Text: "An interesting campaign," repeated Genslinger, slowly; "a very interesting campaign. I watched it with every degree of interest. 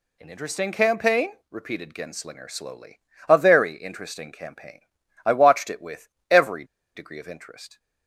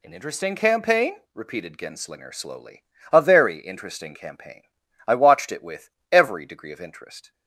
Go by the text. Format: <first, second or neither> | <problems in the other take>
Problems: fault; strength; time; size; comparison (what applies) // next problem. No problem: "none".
second | pauses between "with" and "every"; slight; at 6.0 s; 0.20 s long; slight in the second // pauses between "every" and "degree"; slight; at 6.6 s; 0.31 s long